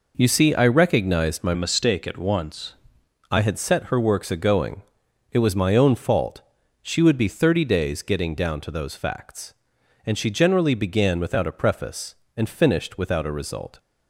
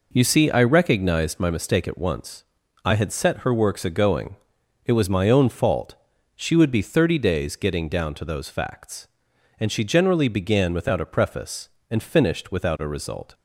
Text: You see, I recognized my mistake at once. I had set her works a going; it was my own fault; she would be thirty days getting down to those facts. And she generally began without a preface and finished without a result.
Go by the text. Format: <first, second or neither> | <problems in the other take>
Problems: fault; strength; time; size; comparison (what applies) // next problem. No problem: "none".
second | changes voice from "mistake" to "once"; from 1.5 to 2.7 s; 1.2 s long